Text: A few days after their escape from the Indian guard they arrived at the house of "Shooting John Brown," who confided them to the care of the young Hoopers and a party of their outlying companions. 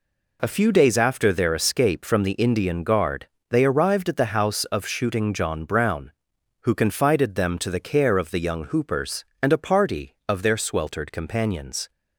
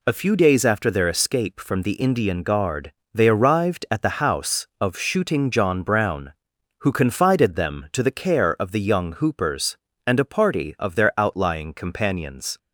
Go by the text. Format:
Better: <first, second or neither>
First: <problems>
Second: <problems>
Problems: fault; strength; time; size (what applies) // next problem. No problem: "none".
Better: second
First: pauses between "guard" and "they"; slight; at 3.2 s; 0.24 s long // says "sweltered" for "outlying"; at 10.5 s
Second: pauses between "guard" and "they"; slight; at 2.9 s; 0.22 s long